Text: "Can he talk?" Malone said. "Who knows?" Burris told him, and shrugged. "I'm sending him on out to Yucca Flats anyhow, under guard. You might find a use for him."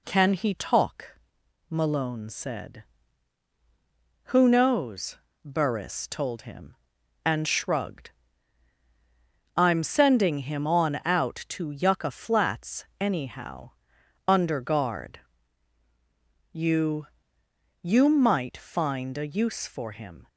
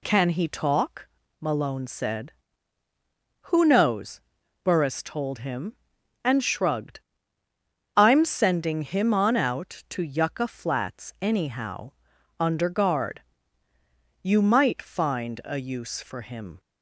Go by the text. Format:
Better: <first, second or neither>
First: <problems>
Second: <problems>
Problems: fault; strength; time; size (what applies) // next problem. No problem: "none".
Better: second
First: pauses between "Flats" and "anyhow"; slight; at 12.8 s; 0.16 s long // says "You" twice; at 17.8 s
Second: none